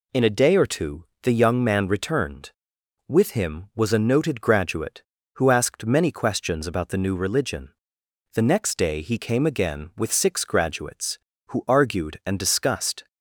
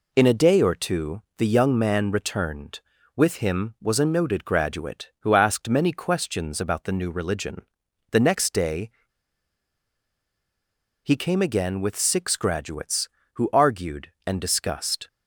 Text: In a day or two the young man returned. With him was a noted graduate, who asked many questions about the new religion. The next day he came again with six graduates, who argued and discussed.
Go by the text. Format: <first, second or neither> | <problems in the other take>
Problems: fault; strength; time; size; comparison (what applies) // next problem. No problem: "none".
first | pauses between "two" and "the"; slight; at 1.2 s; 0.16 s long; slight in the first // pauses between "day" and "he"; strong; at 8.8 s; 2.1 s long